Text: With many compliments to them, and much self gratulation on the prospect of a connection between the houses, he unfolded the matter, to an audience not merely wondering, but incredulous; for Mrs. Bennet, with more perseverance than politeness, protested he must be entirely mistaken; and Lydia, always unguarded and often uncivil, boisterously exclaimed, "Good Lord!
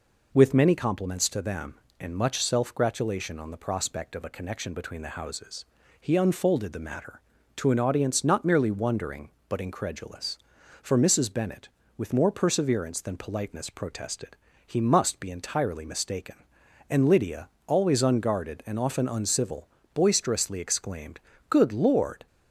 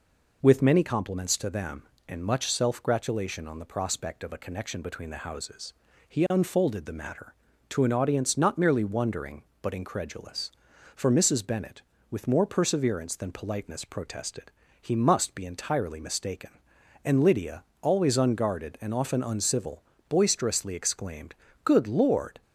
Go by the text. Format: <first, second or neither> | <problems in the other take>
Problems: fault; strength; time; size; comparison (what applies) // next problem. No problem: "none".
neither | pauses between "protested" and "he"; slight; the same in both